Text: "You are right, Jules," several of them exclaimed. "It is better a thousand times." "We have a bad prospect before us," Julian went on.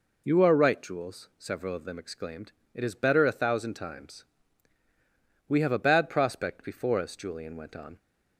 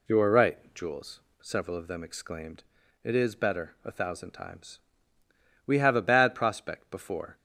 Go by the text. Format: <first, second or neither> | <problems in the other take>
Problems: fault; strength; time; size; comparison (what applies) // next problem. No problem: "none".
first | stops before "us Julian went on"; at 7.3 s